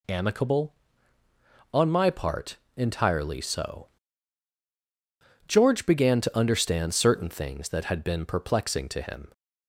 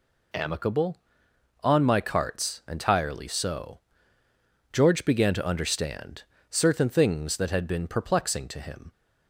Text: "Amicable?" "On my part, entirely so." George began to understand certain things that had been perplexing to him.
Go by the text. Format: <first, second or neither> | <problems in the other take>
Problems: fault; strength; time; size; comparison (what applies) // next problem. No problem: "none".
first | says "carts" for "part"; at 1.9 s // pauses between "understand" and "certain"; slight; at 6.2 s; 0.26 s long